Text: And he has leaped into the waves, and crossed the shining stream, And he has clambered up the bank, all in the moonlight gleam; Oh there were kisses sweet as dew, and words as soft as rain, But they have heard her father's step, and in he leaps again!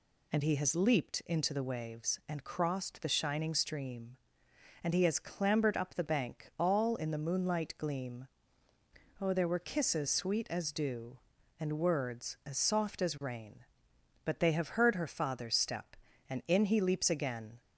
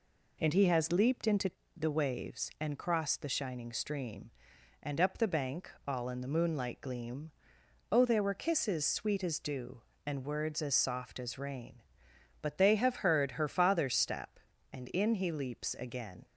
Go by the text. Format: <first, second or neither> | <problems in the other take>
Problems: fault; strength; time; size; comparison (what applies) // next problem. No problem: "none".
first | pauses between "into" and "the"; slight; at 1.5 s; 0.24 s long // skips "he has clambered"; at 4.9 s